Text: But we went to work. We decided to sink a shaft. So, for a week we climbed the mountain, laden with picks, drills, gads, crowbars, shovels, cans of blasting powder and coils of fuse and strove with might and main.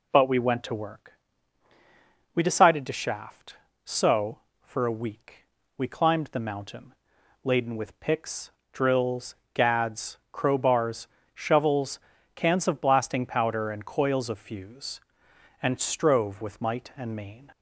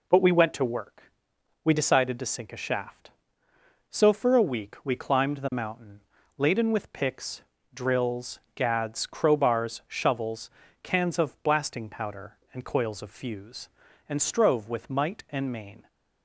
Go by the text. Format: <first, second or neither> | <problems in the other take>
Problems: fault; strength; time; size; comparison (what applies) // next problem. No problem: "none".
second | skips "sink a"; at 2.9 s // pauses between "week" and "we"; at 5.3 s; 0.40 s long